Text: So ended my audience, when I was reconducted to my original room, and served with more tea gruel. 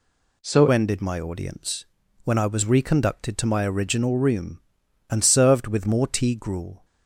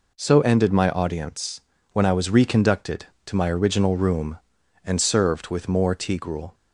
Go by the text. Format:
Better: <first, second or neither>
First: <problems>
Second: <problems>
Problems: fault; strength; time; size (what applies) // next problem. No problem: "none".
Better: second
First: changes voice at "ended"; from 0.7 s on; 6.1 s long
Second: none